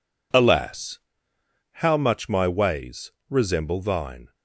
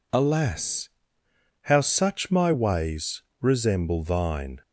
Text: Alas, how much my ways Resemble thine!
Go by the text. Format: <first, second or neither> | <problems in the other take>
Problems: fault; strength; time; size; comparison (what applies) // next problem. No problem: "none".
first | says "such" for "much"; at 1.8 s // pauses between "ways" and "Resemble"; slight; at 3.2 s; 0.18 s long; slight in the first